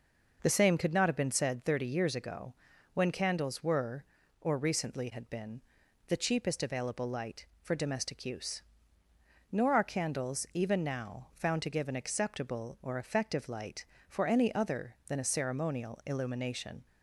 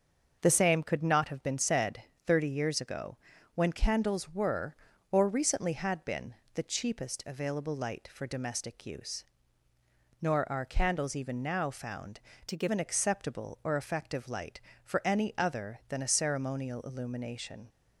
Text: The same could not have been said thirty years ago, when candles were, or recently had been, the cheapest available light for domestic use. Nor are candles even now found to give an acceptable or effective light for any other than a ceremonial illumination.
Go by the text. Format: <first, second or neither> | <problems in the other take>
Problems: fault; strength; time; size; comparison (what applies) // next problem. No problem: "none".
first | starts louder than the rest; until 1.4 s; 6.5 dB // pauses between "said" and "thirty"; slight; at 2.0 s; 0.22 s long // changes voice from "to" to "give"; from 12.4 to 12.6 s; 0.2 s long